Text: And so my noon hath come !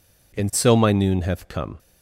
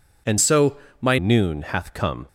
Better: first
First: none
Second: changes voice from "so" to "my"; from 0.3 to 1.1 s; 0.8 s long // pauses between "so" and "my"; slight; at 0.7 s; 0.24 s long

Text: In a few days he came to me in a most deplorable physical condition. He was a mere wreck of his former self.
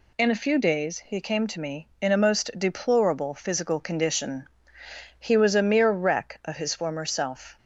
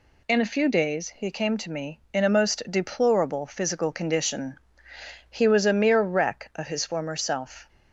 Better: neither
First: none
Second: none

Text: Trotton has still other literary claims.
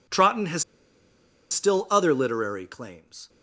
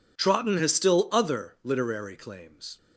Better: second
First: pauses between "has" and "still"; noticeable; at 0.6 s; 0.87 s long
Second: none

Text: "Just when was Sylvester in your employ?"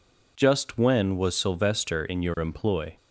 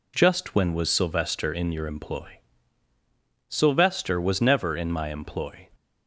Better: first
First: none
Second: goes on to say "Sylvester was never in my employ"; strong; from 3.4 s on; 2.2 s long

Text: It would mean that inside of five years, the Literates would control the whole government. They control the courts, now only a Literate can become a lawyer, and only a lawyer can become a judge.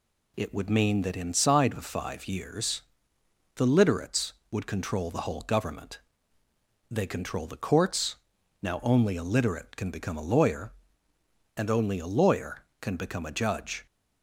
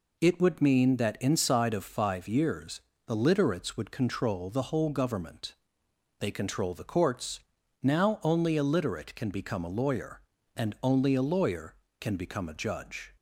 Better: neither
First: none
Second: none

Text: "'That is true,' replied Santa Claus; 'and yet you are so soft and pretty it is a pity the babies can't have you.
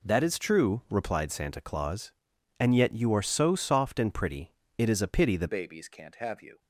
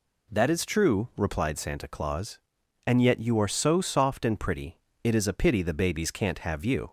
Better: second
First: pauses between "pretty" and "it"; slight; at 4.5 s; 0.26 s long // changes voice at "babies"; from 5.4 s on; 1.1 s long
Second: pauses between "pretty" and "it"; slight; at 4.7 s; 0.26 s long

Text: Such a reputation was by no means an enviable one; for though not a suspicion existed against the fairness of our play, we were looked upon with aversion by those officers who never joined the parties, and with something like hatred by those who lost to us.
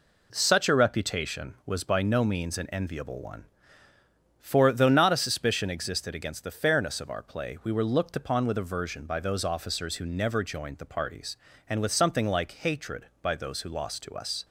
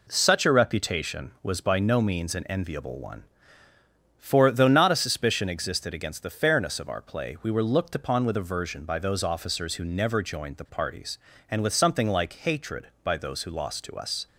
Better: neither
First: none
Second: none

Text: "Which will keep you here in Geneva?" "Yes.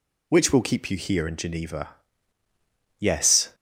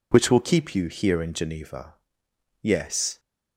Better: neither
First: none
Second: none

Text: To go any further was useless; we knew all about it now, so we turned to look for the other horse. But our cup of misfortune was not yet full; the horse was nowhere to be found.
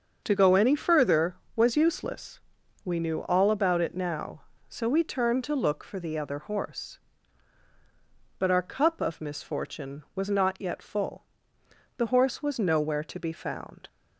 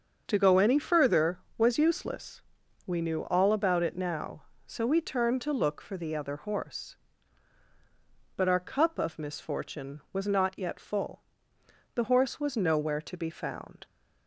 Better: neither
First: starts louder than the rest; until 1.2 s; 6.5 dB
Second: starts louder than the rest; until 1.2 s; 6.5 dB

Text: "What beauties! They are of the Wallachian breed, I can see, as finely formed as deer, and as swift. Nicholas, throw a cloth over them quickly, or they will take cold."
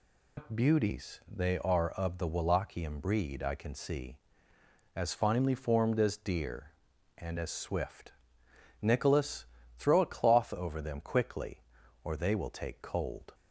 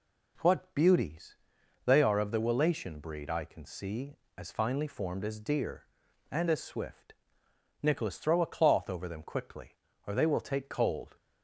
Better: second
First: loses the start of "What"; at 0.3 s; 115 ms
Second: none

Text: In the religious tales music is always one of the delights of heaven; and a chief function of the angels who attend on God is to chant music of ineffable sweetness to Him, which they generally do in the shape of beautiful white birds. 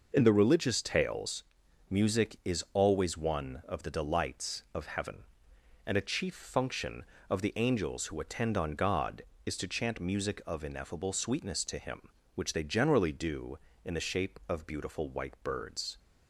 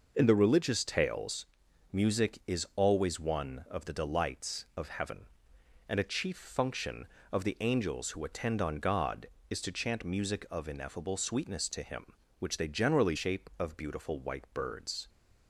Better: first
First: pauses between "tales" and "music"; noticeable; at 1.4 s; 0.46 s long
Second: pauses between "tales" and "music"; noticeable; at 1.4 s; 0.46 s long // skips "do in the"; at 13.1 s

